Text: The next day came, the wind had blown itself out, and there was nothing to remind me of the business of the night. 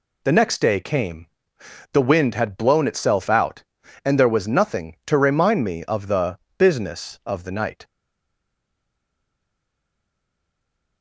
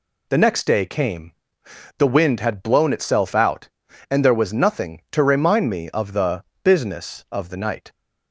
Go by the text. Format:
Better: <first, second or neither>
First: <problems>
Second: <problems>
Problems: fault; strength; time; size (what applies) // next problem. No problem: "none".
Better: second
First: pauses between "the" and "business"; slight; at 6.3 s; 0.20 s long // stays silent after the last word; strong; from 7.8 s on; 3.2 s long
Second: pauses between "the" and "business"; slight; at 6.4 s; 0.20 s long